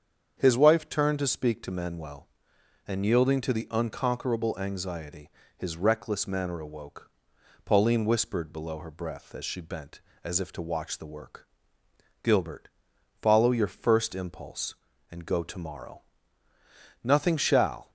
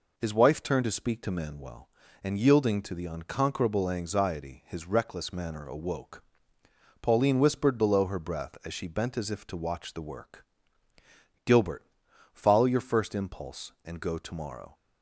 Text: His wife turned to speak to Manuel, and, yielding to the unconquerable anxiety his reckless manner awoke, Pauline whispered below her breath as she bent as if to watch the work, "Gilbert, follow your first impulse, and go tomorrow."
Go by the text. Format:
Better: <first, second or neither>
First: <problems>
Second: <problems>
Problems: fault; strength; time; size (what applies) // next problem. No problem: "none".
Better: second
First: starts louder than the rest; strong; until 1.3 s; 7.5 dB // pauses between "anxiety" and "his"; slight; at 5.3 s; 0.26 s long // goes on to say "Nothing shall"; noticeable; from 17.0 s on; 0.88 s long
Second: none